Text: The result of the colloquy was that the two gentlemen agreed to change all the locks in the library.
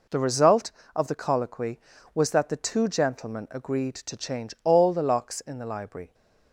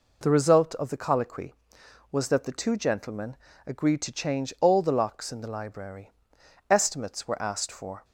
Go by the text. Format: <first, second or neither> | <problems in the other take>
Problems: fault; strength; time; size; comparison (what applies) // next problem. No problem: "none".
first | pauses between "gentlemen" and "agreed"; slight; at 3.3 s; 0.30 s long // goes on to say "Estimates were asked for"; from 6.7 s on; 1.3 s long